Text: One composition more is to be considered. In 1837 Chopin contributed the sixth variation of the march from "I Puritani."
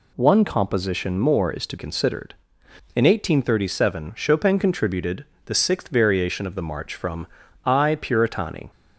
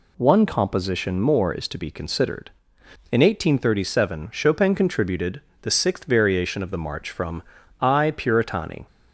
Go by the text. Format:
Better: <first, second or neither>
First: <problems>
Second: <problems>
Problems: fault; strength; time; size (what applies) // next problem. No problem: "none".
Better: second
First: skips "be"; at 1.7 s // pauses between "contributed" and "the"; slight; at 5.2 s; 0.22 s long // pauses between "from" and "I"; at 7.2 s; 0.40 s long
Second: pauses between "contributed" and "the"; slight; at 5.4 s; 0.22 s long // pauses between "from" and "I"; at 7.4 s; 0.40 s long